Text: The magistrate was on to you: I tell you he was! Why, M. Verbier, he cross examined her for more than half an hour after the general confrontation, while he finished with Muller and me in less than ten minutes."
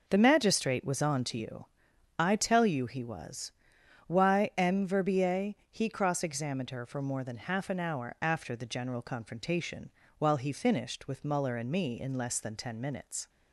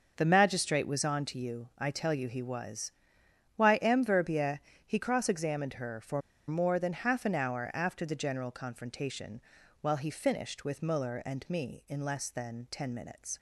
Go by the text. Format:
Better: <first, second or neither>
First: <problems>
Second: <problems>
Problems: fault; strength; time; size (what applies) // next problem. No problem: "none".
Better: first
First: none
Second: starts louder than the rest; until 1.1 s; 6.5 dB // pauses between "for" and "more"; slight; at 6.2 s; 0.26 s long